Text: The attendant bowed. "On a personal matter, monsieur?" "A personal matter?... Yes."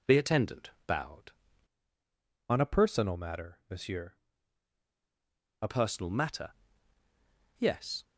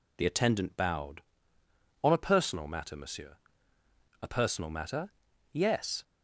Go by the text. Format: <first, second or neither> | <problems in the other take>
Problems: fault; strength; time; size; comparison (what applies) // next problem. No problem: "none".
second | pauses between "attendant" and "bowed"; slight; at 0.6 s; 0.16 s long // changes voice from "On" to "A"; from 2.4 to 5.6 s; 3.2 s long